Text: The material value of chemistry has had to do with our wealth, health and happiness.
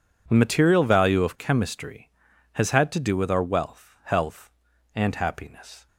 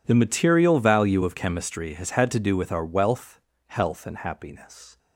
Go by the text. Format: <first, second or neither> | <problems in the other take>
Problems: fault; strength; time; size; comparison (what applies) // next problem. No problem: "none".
neither | none